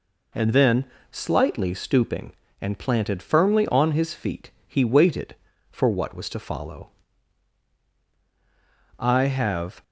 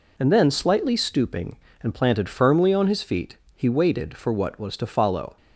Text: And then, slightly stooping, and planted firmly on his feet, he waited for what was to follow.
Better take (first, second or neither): second